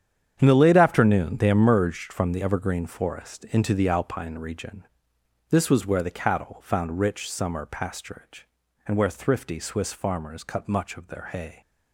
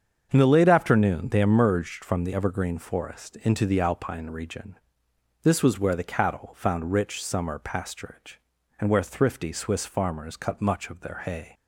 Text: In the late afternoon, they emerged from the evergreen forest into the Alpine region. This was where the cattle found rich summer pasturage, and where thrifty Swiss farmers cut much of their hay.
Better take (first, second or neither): second